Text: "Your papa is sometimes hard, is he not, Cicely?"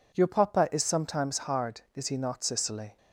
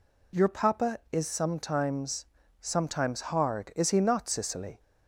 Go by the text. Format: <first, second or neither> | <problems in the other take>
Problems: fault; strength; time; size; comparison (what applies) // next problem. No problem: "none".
first | says "sometimes" twice; at 2.5 s